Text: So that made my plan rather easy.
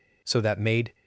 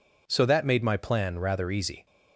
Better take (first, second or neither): second